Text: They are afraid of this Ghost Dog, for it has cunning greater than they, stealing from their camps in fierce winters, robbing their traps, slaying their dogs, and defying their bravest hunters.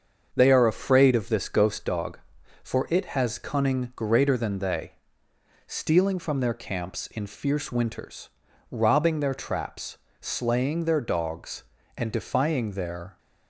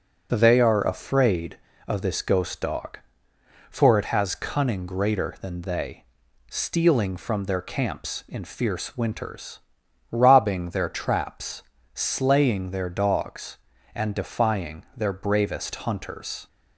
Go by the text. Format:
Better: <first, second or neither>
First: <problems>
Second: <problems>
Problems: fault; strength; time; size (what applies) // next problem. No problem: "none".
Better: second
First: starts louder than the rest; until 1.3 s; 6.5 dB // stops before "bravest hunters"; at 13.1 s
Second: none